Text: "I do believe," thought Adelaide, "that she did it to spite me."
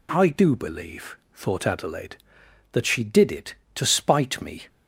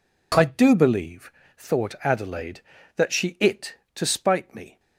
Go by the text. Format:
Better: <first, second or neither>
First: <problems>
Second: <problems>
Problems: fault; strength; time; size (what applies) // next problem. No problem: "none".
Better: first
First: none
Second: skips "did"; at 3.3 s